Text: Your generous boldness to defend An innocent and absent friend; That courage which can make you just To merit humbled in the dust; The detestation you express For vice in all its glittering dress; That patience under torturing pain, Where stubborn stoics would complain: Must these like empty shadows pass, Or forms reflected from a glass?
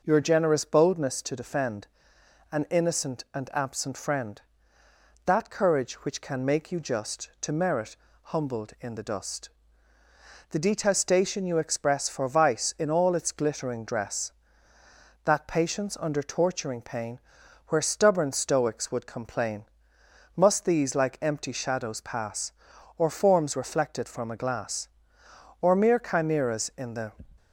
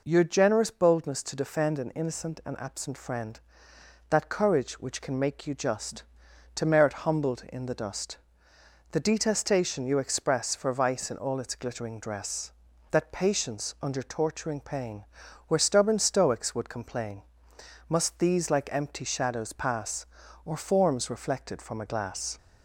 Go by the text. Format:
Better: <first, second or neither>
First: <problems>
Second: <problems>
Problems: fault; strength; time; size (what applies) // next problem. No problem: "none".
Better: second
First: pauses between "defend" and "An"; noticeable; at 1.8 s; 0.66 s long // pauses between "merit" and "humbled"; slight; at 7.9 s; 0.26 s long // goes on to say "Or mere chimeras in the"; from 25.5 s on; 1.5 s long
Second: none